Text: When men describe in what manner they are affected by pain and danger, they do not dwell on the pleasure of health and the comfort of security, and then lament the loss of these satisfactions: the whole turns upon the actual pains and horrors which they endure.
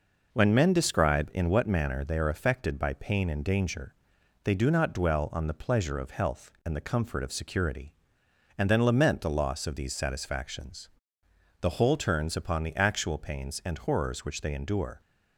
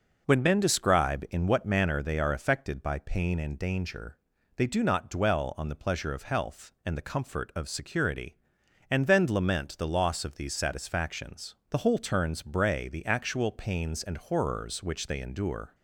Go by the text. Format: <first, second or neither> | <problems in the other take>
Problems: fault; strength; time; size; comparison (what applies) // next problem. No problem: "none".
first | says "bray" for "upon"; at 12.4 s